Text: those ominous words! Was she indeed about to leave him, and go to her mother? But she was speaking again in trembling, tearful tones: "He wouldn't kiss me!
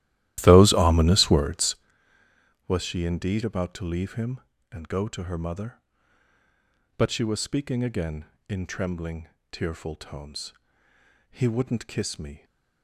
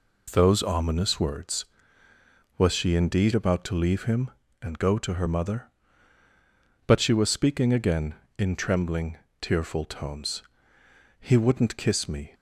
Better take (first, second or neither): second